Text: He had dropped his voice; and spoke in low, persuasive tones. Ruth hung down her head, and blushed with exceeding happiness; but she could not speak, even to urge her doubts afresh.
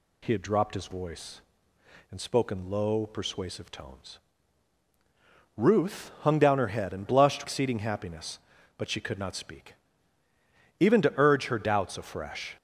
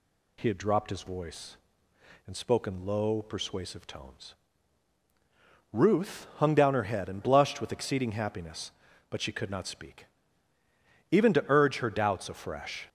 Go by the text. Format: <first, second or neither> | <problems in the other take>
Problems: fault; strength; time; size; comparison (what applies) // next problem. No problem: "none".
second | skips "with"; at 7.4 s